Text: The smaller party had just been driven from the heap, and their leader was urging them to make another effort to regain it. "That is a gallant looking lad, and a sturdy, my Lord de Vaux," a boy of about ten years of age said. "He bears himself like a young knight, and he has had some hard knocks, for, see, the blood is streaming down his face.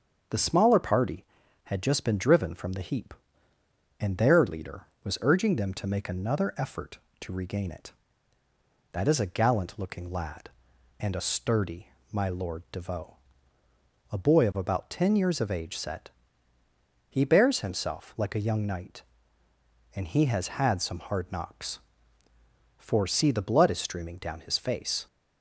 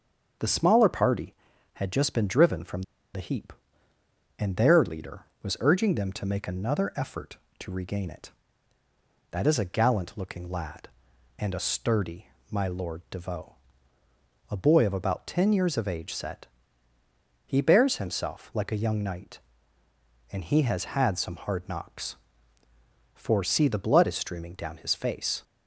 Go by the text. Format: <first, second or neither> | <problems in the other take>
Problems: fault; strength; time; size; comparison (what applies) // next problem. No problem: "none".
first | starts louder than the rest; until 1.8 s; 6.5 dB; also in the first // pauses between "from" and "the"; slight; at 2.8 s; 0.32 s long